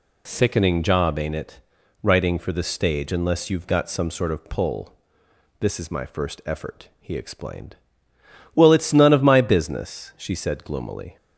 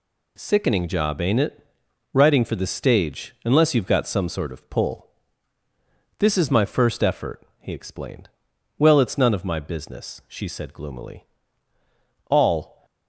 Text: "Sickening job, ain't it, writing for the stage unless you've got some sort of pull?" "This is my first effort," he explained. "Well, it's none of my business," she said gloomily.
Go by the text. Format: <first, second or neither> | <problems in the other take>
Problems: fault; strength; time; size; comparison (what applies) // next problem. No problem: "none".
first | goes on to say "All"; from 12.2 s on; 0.56 s long